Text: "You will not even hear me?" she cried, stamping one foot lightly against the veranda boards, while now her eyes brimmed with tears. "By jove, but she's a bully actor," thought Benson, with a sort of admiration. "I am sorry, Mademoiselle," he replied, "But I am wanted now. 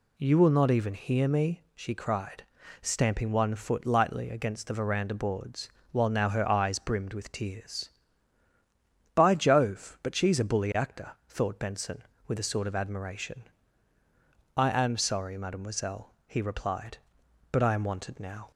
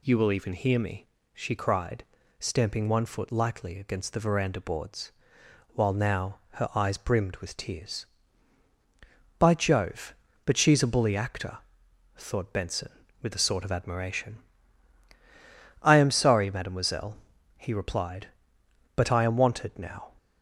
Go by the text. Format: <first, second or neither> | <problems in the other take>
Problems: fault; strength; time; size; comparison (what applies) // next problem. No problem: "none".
first | skips "not"; at 0.3 s // pauses between "now" and "her"; slight; at 6.3 s; 0.16 s long